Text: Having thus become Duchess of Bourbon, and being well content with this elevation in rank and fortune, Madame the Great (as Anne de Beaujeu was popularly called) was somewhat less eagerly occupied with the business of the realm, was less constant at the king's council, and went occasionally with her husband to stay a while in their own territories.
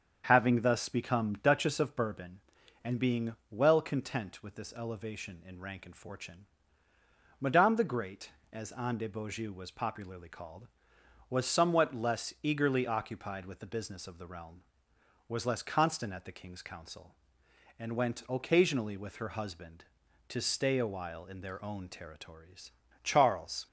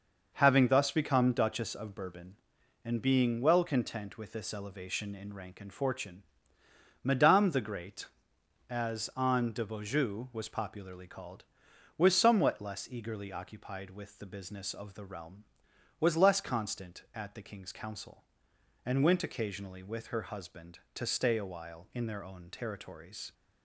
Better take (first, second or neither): second